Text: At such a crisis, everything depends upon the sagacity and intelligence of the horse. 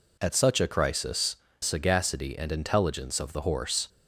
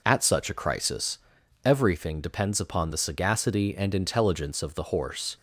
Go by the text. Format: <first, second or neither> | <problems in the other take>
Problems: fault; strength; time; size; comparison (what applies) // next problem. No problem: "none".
second | skips "everything depends upon the"; at 1.4 s